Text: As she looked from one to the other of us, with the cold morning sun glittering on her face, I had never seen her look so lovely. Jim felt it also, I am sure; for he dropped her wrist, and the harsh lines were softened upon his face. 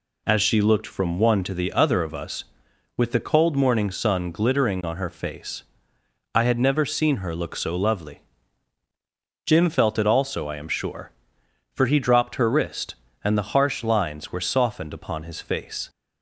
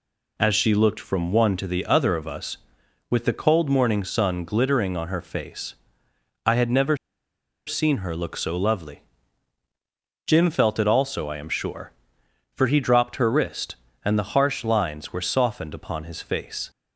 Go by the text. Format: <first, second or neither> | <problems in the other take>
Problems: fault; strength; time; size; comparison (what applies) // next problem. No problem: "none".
first | pauses between "never" and "seen"; noticeable; at 6.9 s; 0.70 s long